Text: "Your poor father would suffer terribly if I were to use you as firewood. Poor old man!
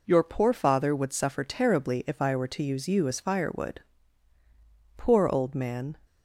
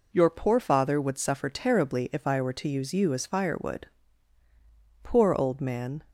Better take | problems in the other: neither | none

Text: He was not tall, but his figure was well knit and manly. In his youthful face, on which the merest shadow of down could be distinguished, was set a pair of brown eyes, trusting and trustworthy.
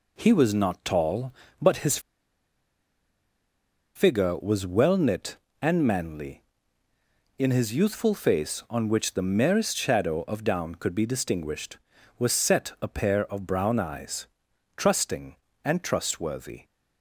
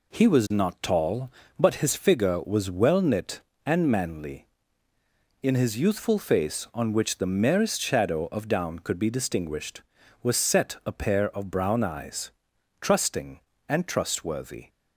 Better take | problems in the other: second | pauses between "his" and "figure"; strong; at 1.9 s; 1.9 s long

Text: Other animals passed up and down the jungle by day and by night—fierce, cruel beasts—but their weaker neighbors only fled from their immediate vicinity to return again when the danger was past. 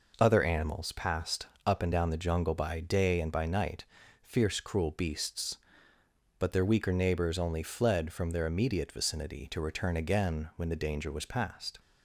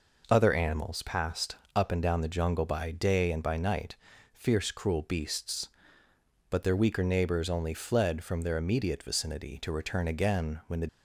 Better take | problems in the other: first | pauses between "passed" and "up"; slight; at 1.5 s; 0.18 s long; slight in the first // stops before "danger was past"; at 10.8 s

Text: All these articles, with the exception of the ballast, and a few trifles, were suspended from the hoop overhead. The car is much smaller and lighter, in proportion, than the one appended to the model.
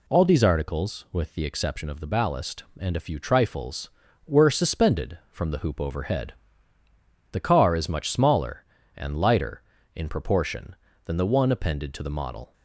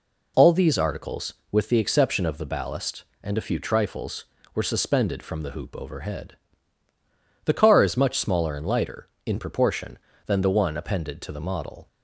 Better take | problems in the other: neither | none

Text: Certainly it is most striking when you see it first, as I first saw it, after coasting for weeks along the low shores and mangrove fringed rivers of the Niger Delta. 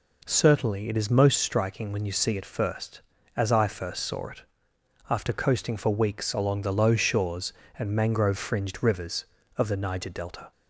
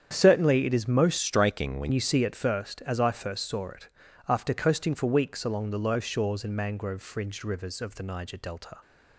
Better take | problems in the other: first | starts louder than the rest; strong; until 1.1 s; 8.5 dB // changes voice from "striking" to "when"; from 1.1 to 1.9 s; 0.8 s long

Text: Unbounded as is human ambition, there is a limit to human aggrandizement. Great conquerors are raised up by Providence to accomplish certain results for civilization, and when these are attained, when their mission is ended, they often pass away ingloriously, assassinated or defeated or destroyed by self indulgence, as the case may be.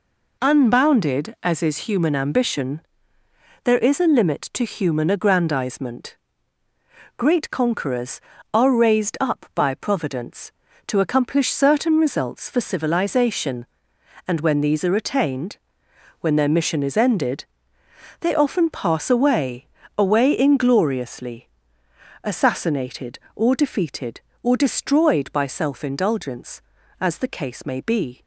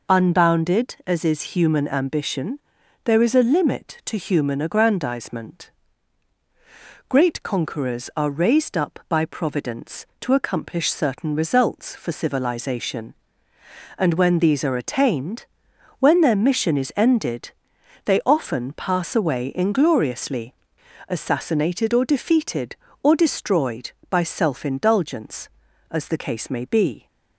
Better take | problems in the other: second | says "away" twice; at 19.9 s

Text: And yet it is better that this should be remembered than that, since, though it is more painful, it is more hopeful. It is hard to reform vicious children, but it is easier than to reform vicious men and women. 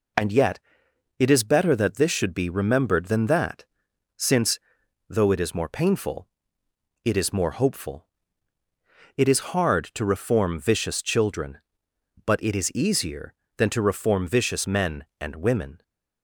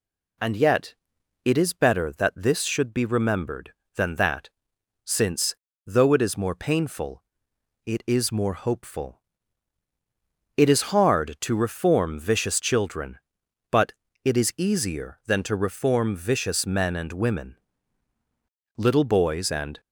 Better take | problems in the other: first | pauses between "yet" and "it"; noticeable; at 0.9 s; 0.50 s long; noticeable in the first // pauses between "but" and "it"; slight; at 13.9 s; 0.30 s long // goes on to say "Little boys and"; noticeable; from 18.7 s on; 1.0 s long

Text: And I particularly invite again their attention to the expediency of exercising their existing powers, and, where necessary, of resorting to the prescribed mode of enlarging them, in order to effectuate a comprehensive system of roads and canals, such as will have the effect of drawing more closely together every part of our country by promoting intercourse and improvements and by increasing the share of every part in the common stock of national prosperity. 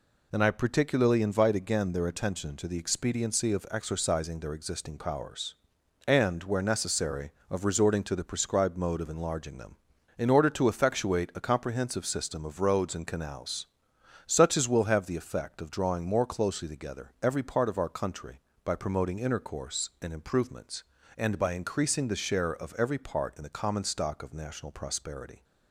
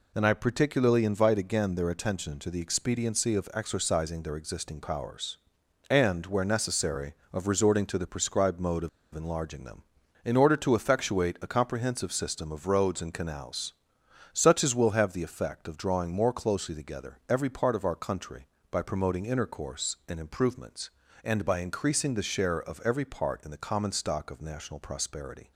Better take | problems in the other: first | pauses between "of" and "enlarging"; slight; at 8.8 s; 0.26 s long

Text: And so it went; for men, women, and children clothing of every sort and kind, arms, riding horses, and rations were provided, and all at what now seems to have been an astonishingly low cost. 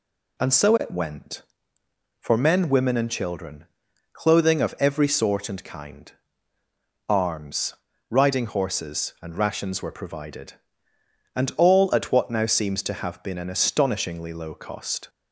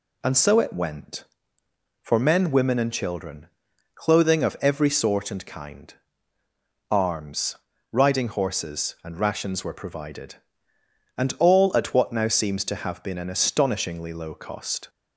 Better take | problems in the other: neither | pauses between "children" and "clothing"; noticeable; the same in both

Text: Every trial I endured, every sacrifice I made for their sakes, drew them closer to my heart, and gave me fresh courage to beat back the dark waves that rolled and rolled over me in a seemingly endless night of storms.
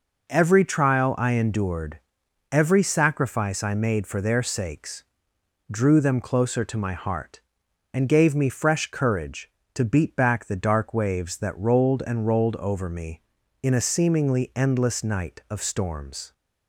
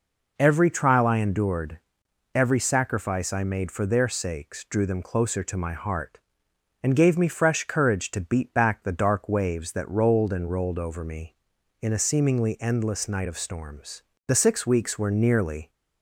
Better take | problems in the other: first | goes on to say "The six weeks were nearly"; from 14.2 s on; 1.4 s long

